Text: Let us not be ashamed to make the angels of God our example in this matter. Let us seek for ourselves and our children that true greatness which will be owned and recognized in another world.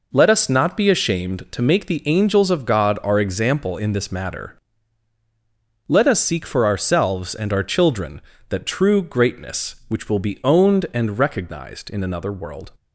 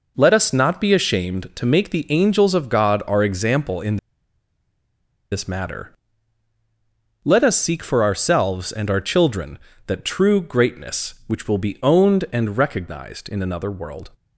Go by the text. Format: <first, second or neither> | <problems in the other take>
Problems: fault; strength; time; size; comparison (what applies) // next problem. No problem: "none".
first | pauses between "in" and "this"; strong; at 3.9 s; 1.3 s long